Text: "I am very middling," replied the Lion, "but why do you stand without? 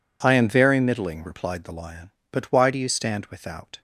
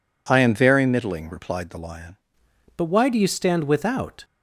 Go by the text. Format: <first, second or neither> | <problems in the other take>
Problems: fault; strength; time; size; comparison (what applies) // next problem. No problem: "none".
first | changes voice at "but"; from 2.7 s on; 1.5 s long